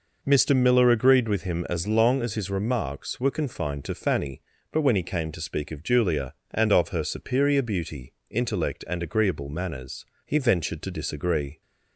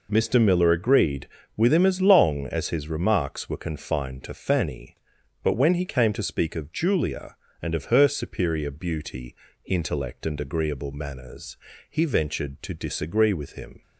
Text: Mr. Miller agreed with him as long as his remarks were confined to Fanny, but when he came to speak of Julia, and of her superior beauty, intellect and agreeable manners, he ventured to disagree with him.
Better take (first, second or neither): second